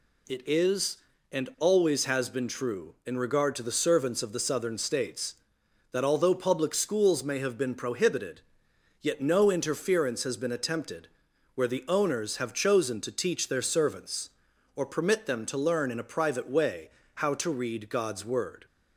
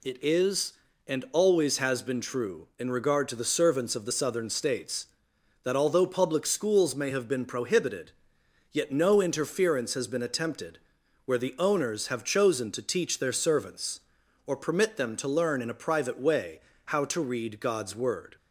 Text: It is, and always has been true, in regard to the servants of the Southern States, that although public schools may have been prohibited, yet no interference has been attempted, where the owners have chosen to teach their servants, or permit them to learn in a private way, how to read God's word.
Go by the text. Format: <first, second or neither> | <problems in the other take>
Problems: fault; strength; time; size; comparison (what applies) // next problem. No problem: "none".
neither | none